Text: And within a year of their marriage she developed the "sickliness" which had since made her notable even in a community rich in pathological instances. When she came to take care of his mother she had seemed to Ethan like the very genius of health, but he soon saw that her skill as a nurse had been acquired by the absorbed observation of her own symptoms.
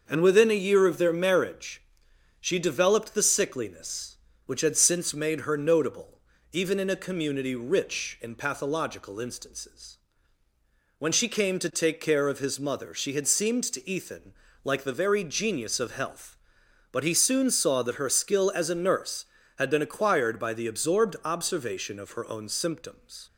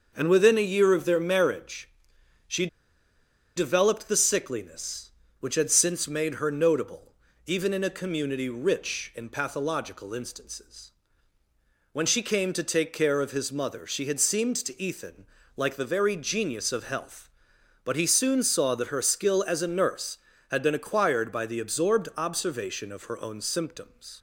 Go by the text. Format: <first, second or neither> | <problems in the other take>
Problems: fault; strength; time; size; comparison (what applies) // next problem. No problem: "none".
first | starts louder than the rest; noticeable; until 1.1 s; 6 dB; noticeable in the first // pauses between "marriage" and "she"; noticeable; at 1.8 s; 0.58 s long; noticeable in the first // pauses between "she" and "developed"; noticeable; at 2.6 s; 0.89 s long // pauses between "notable" and "even"; slight; at 7.1 s; 0.32 s long; slight in the first // pauses between "Ethan" and "like"; slight; at 15.2 s; 0.30 s long; slight in the first